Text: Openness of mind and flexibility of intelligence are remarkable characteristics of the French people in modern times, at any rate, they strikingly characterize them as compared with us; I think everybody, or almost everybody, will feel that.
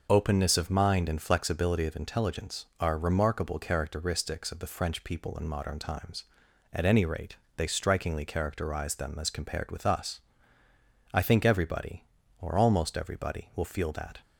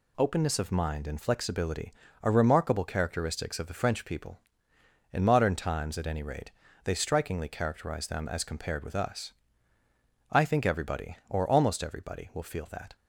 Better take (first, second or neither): first